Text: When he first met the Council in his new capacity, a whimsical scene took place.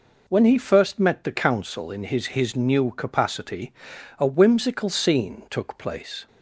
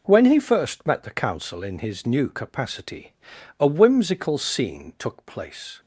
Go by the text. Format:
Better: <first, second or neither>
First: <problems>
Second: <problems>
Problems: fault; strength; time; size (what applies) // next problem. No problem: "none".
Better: second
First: says "his" twice; at 2.2 s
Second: none